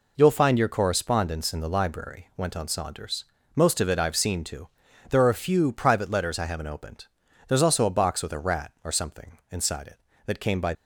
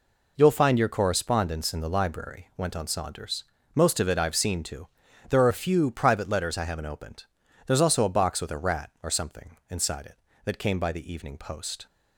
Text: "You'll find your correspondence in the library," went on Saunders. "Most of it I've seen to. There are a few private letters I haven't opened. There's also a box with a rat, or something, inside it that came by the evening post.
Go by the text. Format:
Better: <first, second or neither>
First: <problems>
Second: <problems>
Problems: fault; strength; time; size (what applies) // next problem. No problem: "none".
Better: second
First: stops before "the evening post"; at 10.7 s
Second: none